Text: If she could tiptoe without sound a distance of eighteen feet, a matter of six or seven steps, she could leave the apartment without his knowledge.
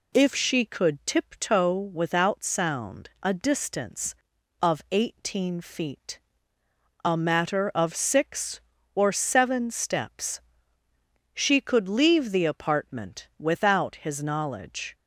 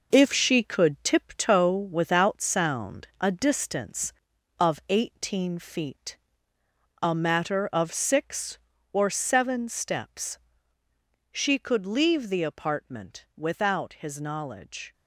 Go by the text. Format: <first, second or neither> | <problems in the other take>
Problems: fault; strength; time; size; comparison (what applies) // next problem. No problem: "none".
first | gets quieter; throughout; 6.5 dB